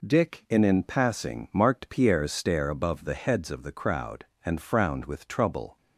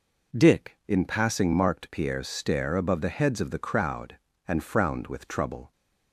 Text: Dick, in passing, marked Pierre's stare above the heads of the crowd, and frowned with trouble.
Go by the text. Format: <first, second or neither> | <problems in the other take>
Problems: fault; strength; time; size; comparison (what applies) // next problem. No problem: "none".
second | says "in" twice; at 0.6 s